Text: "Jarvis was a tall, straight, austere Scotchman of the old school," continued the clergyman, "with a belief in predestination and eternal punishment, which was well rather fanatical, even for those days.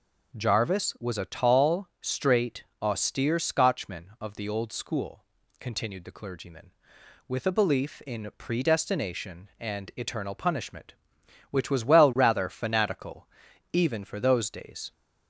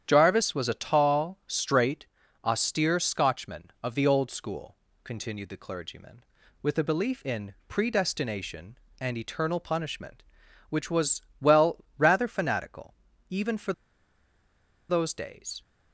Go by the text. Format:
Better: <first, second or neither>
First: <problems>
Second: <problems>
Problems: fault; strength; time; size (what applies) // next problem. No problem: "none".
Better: first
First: none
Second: starts louder than the rest; strong; until 1.0 s; 9 dB // pauses between "was" and "well"; slight; at 11.2 s; 0.18 s long // pauses between "for" and "those"; at 13.7 s; 1.1 s long